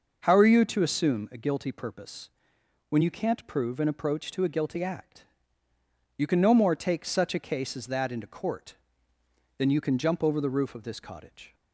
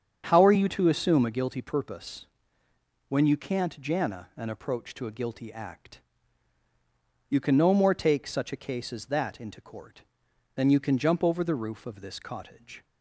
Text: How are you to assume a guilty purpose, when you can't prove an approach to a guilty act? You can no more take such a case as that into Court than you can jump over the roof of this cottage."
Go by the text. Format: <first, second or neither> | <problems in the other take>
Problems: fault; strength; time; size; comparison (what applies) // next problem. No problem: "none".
first | starts louder than the rest; strong; until 1.3 s; 7.5 dB // says "jana" for "prove"; at 3.7 s